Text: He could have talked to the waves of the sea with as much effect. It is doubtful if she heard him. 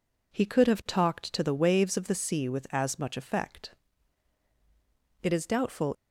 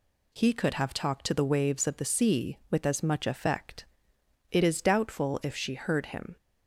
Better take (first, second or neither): second